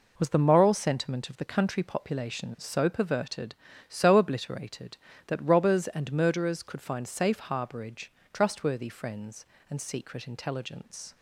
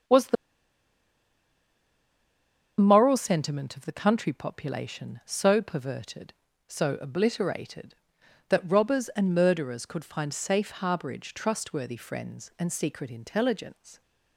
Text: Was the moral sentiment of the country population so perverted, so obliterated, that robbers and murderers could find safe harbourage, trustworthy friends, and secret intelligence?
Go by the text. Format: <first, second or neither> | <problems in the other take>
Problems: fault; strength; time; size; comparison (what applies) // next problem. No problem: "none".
first | starts louder than the rest; strong; until 3.5 s; 8 dB // pauses between "the" and "moral"; strong; at 0.3 s; 2.4 s long